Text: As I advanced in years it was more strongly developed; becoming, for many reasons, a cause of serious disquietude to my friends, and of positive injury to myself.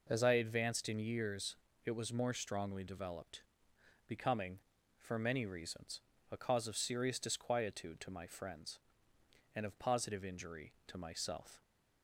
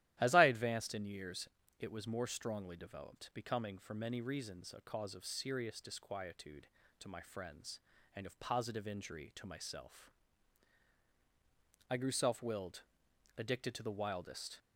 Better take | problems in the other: first | starts louder than the rest; strong; until 1.2 s; 13.5 dB // pauses between "years" and "it"; slight; at 1.4 s; 0.30 s long; slight in the first // goes on to say "I grew self willed addicted to the wildest"; strong; from 11.8 s on; 2.7 s long

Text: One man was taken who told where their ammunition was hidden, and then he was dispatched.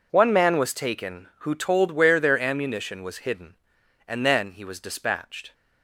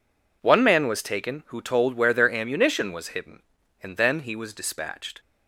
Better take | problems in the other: neither | none

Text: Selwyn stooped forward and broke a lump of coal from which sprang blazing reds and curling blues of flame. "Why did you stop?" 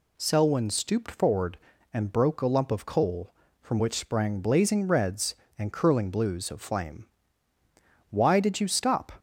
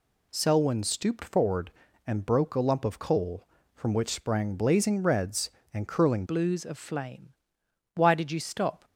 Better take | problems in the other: first | changes voice at "blues"; from 6.2 s on; 2.6 s long

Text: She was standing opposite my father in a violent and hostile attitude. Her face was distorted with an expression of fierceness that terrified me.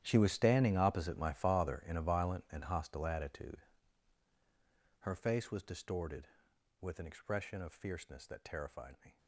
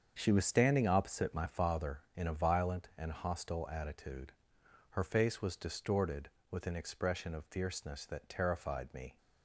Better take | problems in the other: second | gets quieter; strong; throughout; 17 dB // starts louder than the rest; strong; until 1.0 s; 11 dB; strong in the second

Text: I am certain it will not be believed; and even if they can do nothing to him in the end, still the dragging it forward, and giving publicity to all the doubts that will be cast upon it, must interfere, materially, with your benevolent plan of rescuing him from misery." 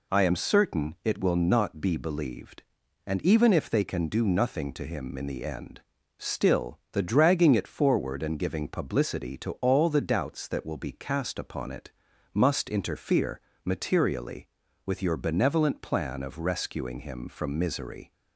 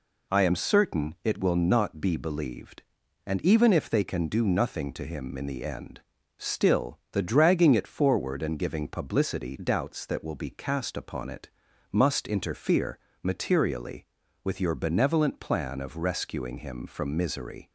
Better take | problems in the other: first | skips "to all the"; at 9.5 s

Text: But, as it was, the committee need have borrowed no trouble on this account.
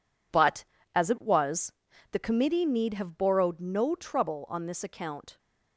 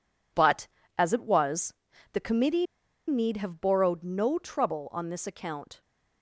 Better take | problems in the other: first | pauses between "committee" and "need"; at 2.6 s; 0.43 s long

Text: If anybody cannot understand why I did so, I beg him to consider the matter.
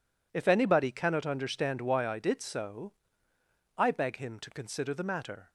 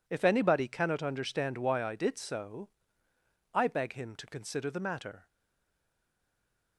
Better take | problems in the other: first | stays silent after the last word; noticeable; from 5.2 s on; 1.5 s long

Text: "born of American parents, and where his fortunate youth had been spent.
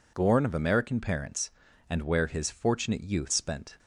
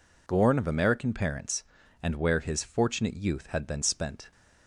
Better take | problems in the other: second | skips "had been"; at 3.3 s

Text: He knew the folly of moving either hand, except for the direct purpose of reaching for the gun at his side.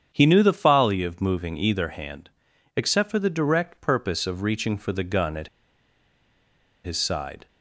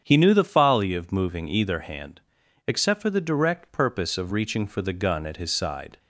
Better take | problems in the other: second | starts louder than the rest; strong; until 1.1 s; 8 dB; strong in the second // pauses between "at" and "his"; strong; at 5.4 s; 1.3 s long

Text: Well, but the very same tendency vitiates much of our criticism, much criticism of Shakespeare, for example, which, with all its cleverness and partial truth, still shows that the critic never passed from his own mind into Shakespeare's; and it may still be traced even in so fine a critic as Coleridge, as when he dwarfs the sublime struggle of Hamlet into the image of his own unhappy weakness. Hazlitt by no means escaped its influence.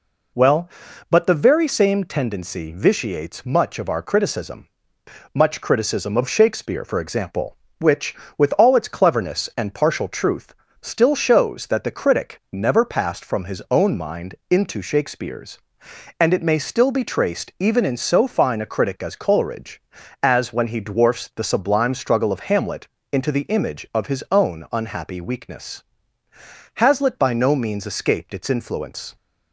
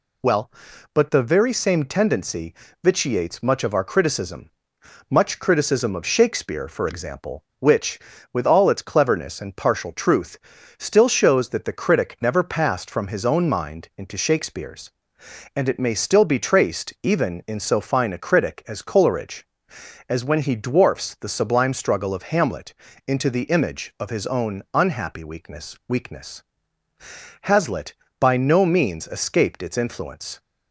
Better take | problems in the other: first | pauses between "tendency" and "vitiates"; slight; at 2.5 s; 0.30 s long // pauses between "Hamlet" and "into"; slight; at 22.7 s; 0.32 s long; slight in the first // says "weakness" twice; at 25.8 s

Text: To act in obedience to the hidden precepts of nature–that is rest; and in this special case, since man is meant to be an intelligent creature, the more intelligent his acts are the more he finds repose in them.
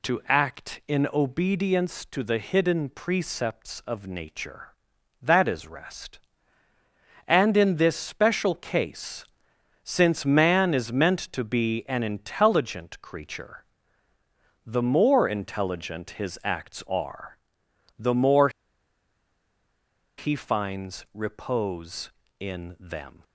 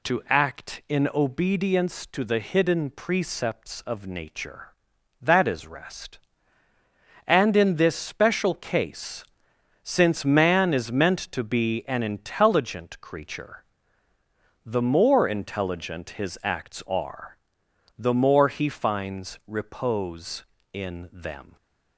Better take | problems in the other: second | pauses between "are" and "the"; noticeable; at 17.3 s; 0.62 s long; noticeable in the second // pauses between "more" and "he"; strong; at 18.4 s; 1.6 s long

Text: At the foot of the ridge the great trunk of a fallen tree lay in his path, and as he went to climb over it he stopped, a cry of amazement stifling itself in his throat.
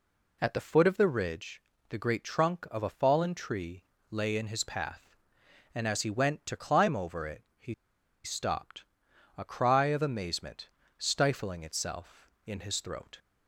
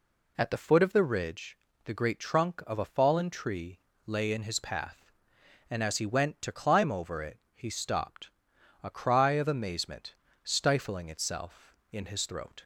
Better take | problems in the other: second | pauses between "ridge" and "the"; slight; at 1.6 s; 0.28 s long; slight in the second // pauses between "tree" and "lay"; slight; at 3.8 s; 0.26 s long; slight in the second // pauses between "it" and "he"; slight; at 7.4 s; 0.16 s long; slight in the second // pauses between "he" and "stopped"; noticeable; at 7.7 s; 0.50 s long // pauses between "amazement" and "stifling"; slight; at 10.7 s; 0.26 s long; slight in the second

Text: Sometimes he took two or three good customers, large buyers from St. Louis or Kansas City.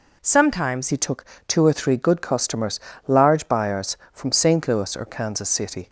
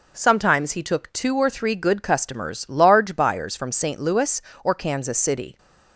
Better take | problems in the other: second | changes voice at "he"; from 0.8 s on; 5.0 s long // pauses between "took" and "two"; slight; at 1.2 s; 0.22 s long

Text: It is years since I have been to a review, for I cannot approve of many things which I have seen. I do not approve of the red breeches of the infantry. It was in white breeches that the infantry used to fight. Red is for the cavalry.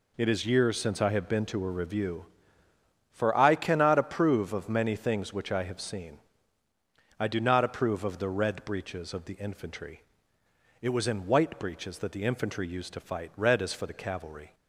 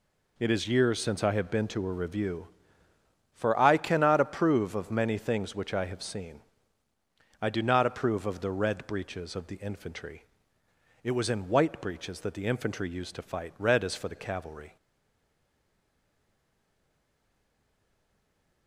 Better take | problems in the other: first | stays silent after the last word; strong; from 14.7 s on; 3.9 s long

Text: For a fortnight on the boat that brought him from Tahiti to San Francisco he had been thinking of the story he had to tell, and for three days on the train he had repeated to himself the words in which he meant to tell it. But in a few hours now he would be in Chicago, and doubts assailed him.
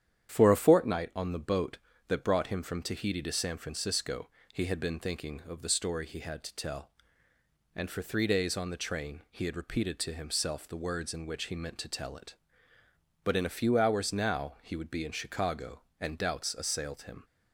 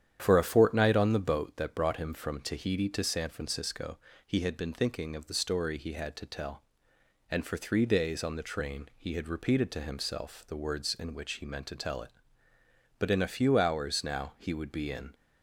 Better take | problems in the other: first | starts louder than the rest; strong; until 1.2 s; 9.5 dB; strong in the first // pauses between "Francisco" and "he"; slight; at 3.9 s; 0.30 s long; slight in the first // stops before "Chicago and doubts assailed him"; at 15.1 s

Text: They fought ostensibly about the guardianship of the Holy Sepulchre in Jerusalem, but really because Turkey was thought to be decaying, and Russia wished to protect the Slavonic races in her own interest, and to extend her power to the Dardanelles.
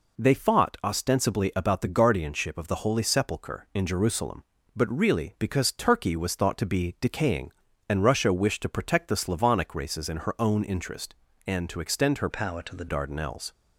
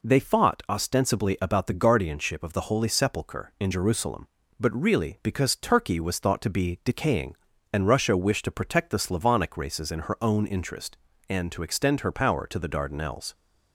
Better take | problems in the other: second | changes voice from "power" to "the"; from 12.3 to 12.8 s; 0.5 s long

